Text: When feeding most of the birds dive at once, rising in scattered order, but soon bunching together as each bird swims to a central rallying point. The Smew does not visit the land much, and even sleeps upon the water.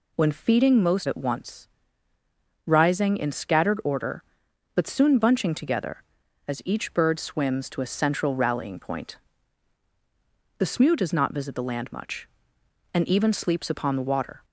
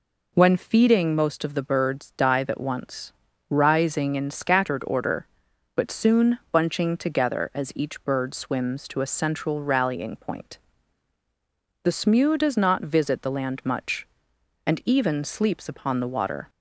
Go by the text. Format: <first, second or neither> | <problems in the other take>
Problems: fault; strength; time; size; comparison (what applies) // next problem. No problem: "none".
second | skips "of the birds dive"; at 1.0 s